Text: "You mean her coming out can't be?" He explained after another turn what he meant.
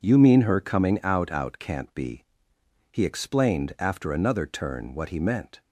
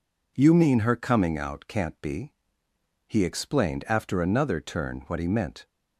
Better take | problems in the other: second | says "out" twice; at 1.2 s

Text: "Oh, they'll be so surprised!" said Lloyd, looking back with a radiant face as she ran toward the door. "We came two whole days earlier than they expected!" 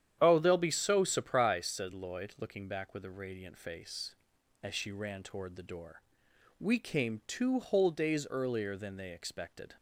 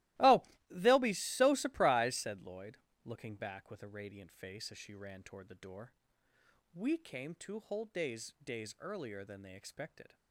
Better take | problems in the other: first | starts louder than the rest; strong; until 1.4 s; 17.5 dB; strong in the first // says "days" twice; at 8.4 s

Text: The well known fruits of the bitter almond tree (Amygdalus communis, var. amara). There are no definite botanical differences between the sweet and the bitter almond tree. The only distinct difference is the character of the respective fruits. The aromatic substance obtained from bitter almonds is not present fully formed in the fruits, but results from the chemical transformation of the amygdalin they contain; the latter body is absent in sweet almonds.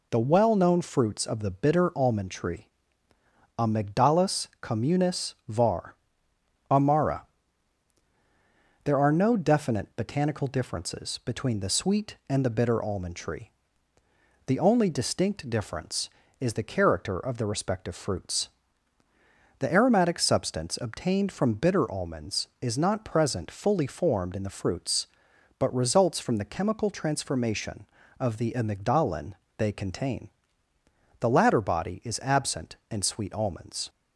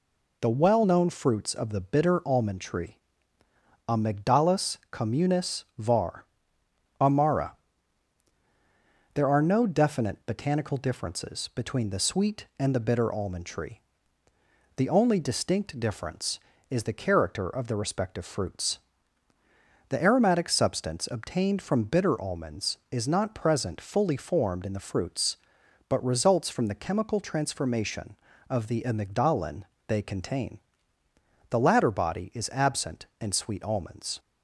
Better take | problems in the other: neither | pauses between "Amygdalus" and "communis"; slight; the same in both // pauses between "amygdalin" and "they"; slight; the same in both

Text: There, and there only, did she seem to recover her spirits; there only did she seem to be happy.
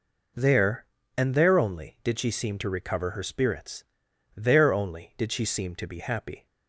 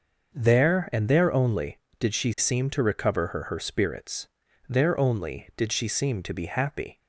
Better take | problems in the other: first | starts louder than the rest; until 1.3 s; 6 dB // says "her" twice; at 3.4 s

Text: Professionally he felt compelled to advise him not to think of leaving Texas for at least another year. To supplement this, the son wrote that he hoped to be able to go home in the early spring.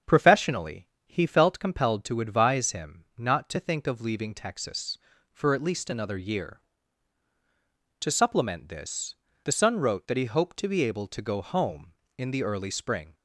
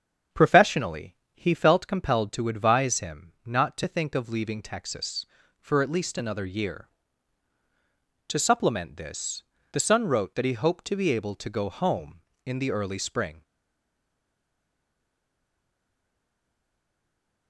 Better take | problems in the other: first | starts louder than the rest; strong; until 1.5 s; 7.5 dB; strong in the first // pauses between "Professionally" and "he"; slight; at 1.1 s; 0.18 s long; slight in the first // stays silent after the last word; strong; from 13.4 s on; 4.0 s long

